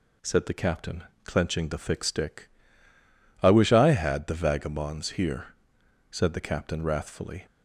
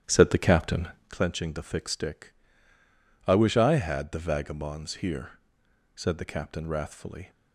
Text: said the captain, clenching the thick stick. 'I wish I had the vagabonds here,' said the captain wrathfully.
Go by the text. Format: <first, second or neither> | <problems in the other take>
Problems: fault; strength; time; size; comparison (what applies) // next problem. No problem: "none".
first | starts louder than the rest; strong; until 1.1 s; 10.5 dB